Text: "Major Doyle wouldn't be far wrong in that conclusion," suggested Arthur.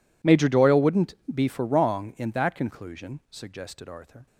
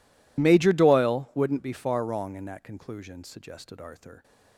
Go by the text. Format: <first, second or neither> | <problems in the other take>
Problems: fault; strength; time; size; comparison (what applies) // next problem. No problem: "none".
second | pauses between "wouldn't" and "be"; slight; at 1.1 s; 0.18 s long // says "for" for "far"; at 1.4 s